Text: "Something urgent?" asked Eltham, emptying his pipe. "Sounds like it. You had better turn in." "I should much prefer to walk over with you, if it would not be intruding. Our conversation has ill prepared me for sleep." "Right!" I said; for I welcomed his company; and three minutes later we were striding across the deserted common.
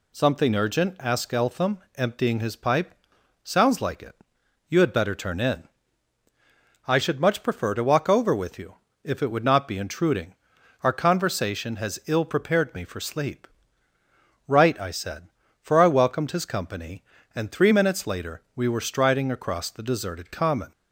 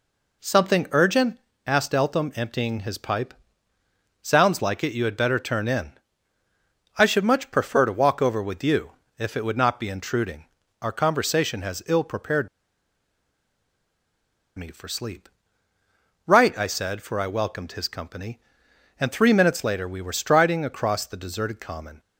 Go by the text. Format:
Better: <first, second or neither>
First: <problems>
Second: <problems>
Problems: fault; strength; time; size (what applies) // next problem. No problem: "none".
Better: first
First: none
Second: pauses between "prepared" and "me"; strong; at 12.4 s; 2.0 s long